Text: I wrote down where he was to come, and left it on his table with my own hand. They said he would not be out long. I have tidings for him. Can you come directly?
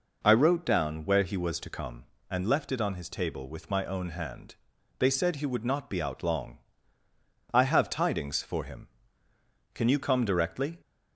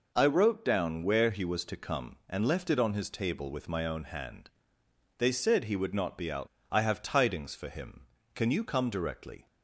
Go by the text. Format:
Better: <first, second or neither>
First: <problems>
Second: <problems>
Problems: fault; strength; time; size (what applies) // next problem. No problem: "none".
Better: first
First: none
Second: skips "long"; at 6.5 s